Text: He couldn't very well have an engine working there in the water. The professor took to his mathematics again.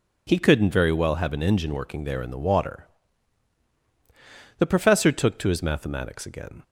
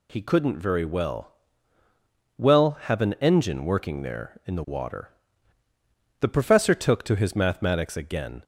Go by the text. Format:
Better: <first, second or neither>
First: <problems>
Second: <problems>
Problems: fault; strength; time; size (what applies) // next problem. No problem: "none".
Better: first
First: none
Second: says "well" twice; at 2.3 s